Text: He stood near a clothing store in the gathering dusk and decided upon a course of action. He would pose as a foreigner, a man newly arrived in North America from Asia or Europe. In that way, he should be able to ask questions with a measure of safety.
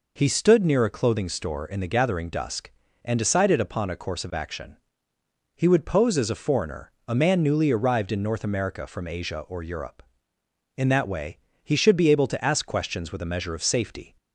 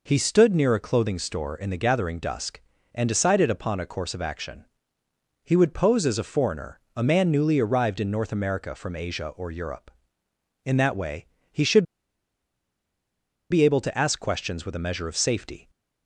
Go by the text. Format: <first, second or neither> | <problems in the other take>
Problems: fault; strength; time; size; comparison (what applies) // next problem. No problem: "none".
first | pauses between "should" and "be"; strong; at 11.8 s; 1.6 s long